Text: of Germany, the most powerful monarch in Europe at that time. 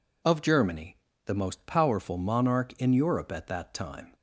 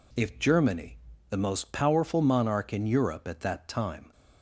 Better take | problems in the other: first | says "if" for "of"; at 0.1 s

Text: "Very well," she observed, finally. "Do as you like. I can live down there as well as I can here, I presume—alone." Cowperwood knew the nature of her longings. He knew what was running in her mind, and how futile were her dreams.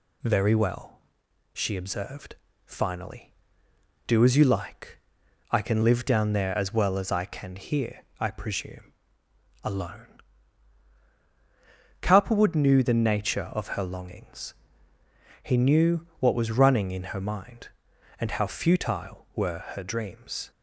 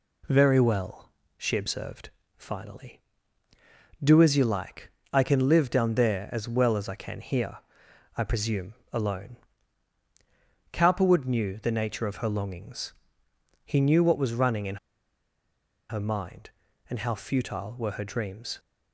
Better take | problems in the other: first | pauses between "in" and "her"; at 14.7 s; 1.1 s long

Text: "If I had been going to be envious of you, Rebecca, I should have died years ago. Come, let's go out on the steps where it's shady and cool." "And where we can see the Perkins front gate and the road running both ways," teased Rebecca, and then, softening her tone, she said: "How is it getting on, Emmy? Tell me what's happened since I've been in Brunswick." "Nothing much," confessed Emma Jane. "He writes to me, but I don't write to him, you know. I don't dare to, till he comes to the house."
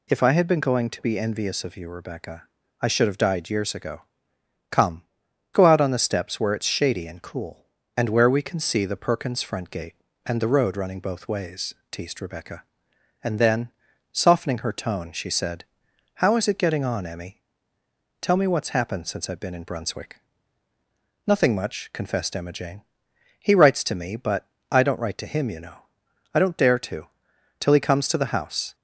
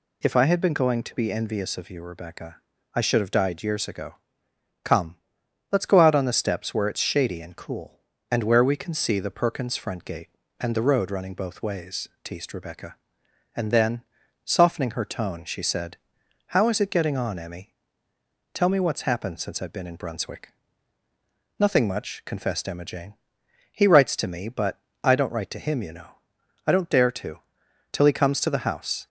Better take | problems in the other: second | skips "let's"; at 5.2 s // pauses between "but" and "I"; slight; at 24.4 s; 0.22 s long; slight in the second

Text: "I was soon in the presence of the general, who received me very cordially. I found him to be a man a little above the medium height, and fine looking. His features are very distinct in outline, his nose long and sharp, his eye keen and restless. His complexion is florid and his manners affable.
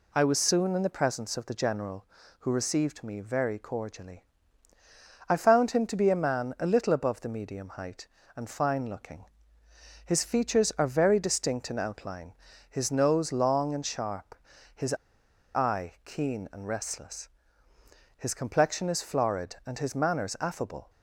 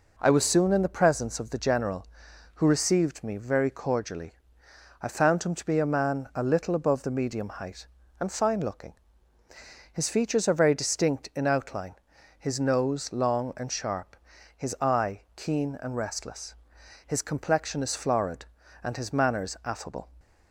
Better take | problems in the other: second | pauses between "his" and "eye"; noticeable; at 14.9 s; 0.62 s long

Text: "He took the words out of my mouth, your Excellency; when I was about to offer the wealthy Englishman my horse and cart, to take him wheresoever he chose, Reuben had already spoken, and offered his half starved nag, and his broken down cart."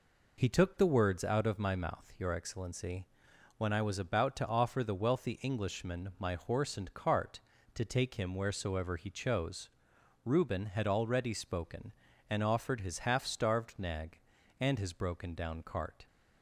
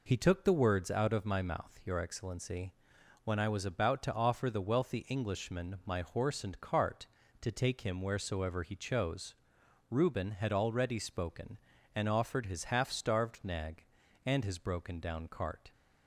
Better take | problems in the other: neither | none

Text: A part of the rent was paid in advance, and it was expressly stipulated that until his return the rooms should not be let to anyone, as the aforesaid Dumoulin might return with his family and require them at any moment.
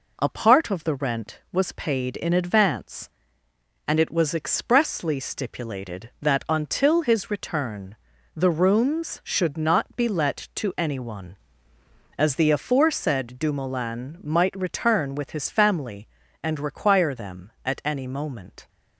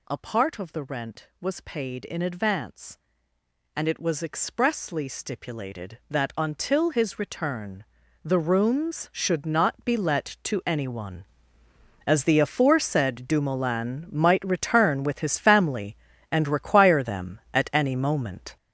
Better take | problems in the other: first | gets louder; strong; throughout; 8.5 dB // pauses between "return" and "the"; at 7.8 s; 0.40 s long; also in the first

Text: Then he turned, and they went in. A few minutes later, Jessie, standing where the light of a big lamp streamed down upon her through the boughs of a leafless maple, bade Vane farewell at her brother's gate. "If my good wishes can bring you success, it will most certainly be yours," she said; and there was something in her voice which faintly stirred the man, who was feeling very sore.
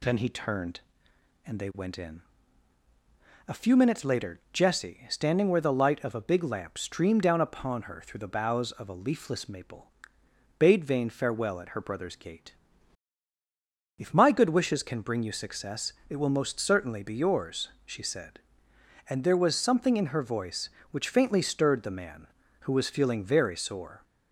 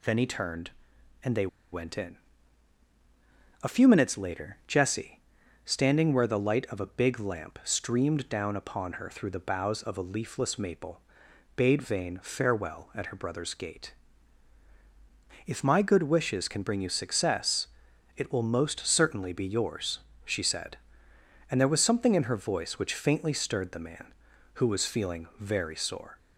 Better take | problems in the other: first | pauses between "they" and "went"; slight; at 1.4 s; 0.25 s long

